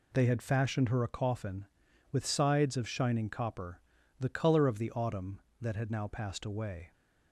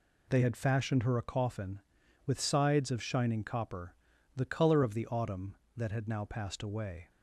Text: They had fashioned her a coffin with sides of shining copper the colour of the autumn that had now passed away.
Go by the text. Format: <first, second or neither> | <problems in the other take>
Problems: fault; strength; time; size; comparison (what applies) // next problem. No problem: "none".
neither | pauses between "copper" and "the"; the same in both